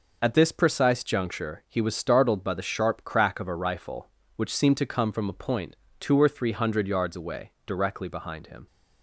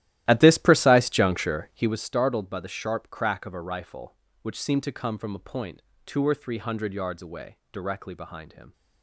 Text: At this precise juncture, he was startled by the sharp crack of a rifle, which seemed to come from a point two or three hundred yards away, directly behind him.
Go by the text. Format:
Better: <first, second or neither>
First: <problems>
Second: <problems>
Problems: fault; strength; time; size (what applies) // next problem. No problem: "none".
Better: first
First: pauses between "point" and "two"; slight; at 5.7 s; 0.24 s long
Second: starts louder than the rest; strong; until 2.0 s; 14.5 dB // pauses between "point" and "two"; slight; at 5.8 s; 0.24 s long